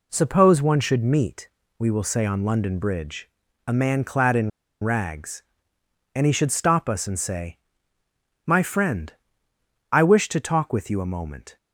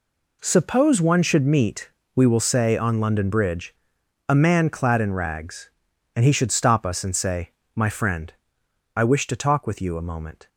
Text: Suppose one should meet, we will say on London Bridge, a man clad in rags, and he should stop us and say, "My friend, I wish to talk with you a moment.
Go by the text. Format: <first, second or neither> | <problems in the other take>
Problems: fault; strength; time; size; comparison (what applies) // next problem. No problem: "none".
second | pauses between "in" and "rags"; slight; at 4.5 s; 0.32 s long